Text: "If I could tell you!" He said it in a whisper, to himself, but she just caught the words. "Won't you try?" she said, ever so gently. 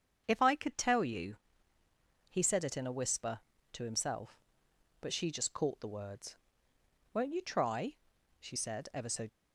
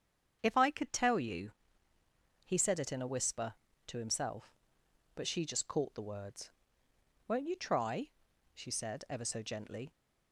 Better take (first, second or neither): second